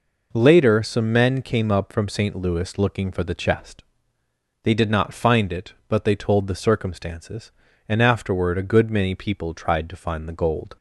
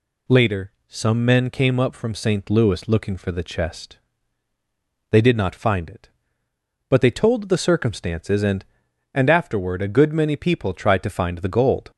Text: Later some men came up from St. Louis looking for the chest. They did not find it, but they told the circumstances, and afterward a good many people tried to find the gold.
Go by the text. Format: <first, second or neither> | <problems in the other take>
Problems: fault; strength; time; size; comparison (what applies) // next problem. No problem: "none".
first | says "and" twice; at 9.1 s